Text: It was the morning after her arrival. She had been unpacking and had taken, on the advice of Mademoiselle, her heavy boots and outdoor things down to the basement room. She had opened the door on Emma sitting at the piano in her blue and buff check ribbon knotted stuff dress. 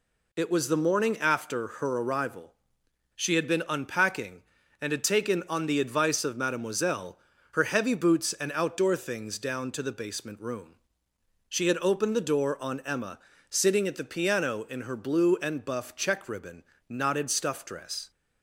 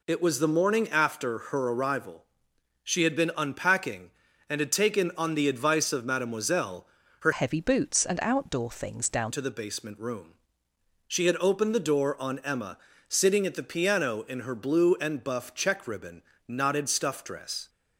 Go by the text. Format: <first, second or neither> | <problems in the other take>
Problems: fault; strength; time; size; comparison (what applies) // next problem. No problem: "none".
first | changes voice from "heavy" to "down"; from 7.3 to 9.3 s; 2.0 s long // pauses between "Emma" and "sitting"; slight; at 12.7 s; 0.28 s long; slight in the first // pauses between "ribbon" and "knotted"; slight; at 16.2 s; 0.24 s long; slight in the first